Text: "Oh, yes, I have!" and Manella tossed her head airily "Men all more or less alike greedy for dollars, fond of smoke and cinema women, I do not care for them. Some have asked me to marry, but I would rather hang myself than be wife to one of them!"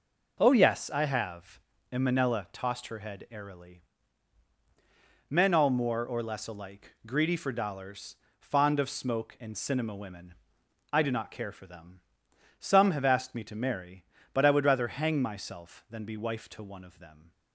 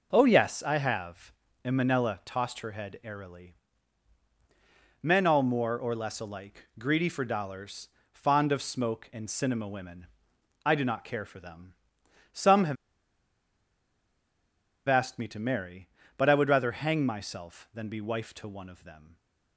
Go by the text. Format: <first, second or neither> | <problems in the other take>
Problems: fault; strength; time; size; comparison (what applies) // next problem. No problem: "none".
first | pauses between "airily" and "Men"; strong; at 3.5 s; 1.4 s long; strong in the first // pauses between "have" and "asked"; strong; at 12.7 s; 2.1 s long